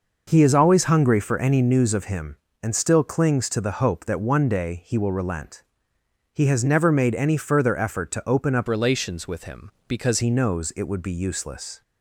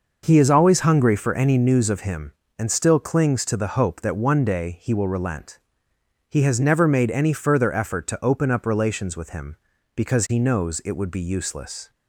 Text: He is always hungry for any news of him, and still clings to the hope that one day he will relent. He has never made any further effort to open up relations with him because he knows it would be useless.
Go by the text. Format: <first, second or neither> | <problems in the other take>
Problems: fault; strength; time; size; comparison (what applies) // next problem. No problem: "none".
second | changes voice from "relations" to "because"; from 8.6 to 10.1 s; 1.5 s long